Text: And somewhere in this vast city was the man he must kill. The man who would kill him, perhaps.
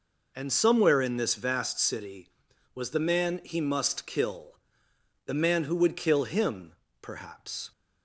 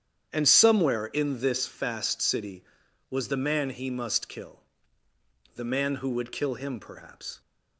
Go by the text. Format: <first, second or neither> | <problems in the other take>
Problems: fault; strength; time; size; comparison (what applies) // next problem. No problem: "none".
first | starts louder than the rest; strong; until 1.3 s; 9 dB // says "fast" for "vast"; at 1.6 s